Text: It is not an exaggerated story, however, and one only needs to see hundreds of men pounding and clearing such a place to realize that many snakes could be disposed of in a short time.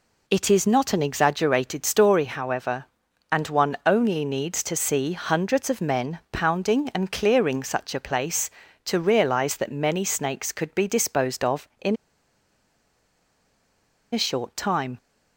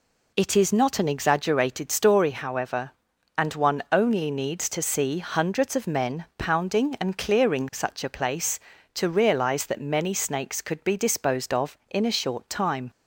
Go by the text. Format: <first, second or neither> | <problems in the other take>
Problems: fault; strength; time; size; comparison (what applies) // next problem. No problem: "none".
second | pauses between "in" and "a"; strong; at 11.9 s; 2.1 s long